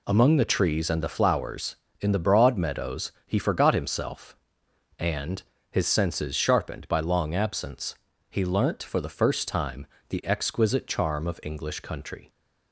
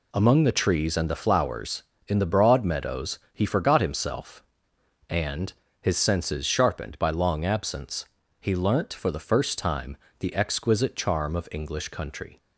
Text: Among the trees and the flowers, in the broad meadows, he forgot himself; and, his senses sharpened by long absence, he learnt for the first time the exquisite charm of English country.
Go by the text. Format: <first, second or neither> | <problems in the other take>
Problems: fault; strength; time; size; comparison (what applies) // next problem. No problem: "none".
neither | pauses between "time" and "the"; slight; the same in both